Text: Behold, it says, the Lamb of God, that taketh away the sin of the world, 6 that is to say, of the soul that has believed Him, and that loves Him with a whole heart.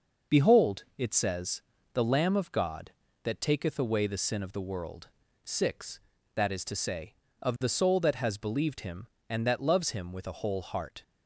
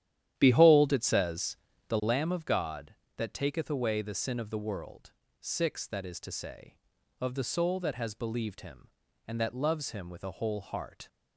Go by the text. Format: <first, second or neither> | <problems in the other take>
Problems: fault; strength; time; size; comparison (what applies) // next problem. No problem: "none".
first | starts louder than the rest; strong; until 2.2 s; 11 dB